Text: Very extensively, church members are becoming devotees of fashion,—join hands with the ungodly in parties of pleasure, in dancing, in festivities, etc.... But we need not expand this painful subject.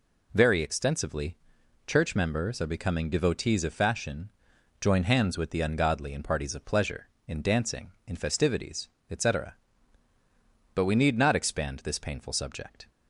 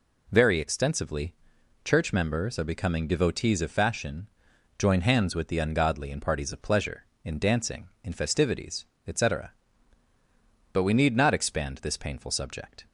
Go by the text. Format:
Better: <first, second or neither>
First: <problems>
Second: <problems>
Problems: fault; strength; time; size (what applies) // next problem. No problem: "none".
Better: neither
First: none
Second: none